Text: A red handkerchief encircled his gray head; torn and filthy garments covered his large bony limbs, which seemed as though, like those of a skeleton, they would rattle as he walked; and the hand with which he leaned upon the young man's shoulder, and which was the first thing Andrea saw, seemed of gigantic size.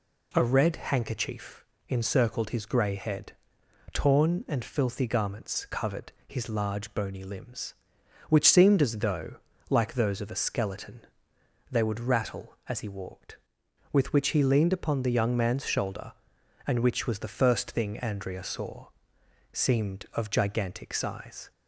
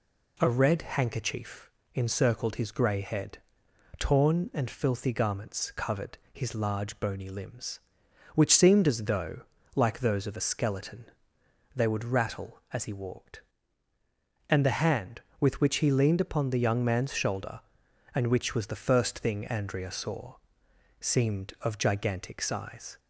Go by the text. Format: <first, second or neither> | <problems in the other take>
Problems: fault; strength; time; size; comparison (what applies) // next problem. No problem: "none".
second | pauses between "handkerchief" and "encircled"; slight; at 1.6 s; 0.28 s long; slight in the second // pauses between "covered" and "his"; slight; at 6.1 s; 0.16 s long; slight in the second // skips "and the hand"; at 13.6 s